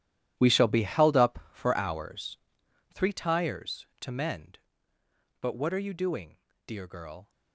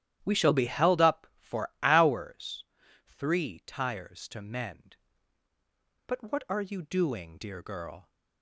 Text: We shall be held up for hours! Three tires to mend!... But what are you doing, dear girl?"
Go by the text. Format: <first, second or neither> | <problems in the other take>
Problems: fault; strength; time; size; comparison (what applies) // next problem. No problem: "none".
second | gets quieter; strong; throughout; 16 dB // starts louder than the rest; strong; until 1.3 s; 12 dB; strong in the second